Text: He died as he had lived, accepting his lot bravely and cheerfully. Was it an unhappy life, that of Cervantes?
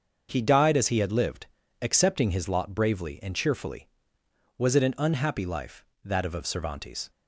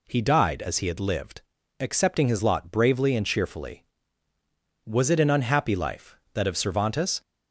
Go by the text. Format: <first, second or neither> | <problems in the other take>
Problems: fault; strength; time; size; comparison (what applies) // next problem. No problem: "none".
second | starts louder than the rest; until 1.3 s; 6.5 dB // says "of" twice; at 6.3 s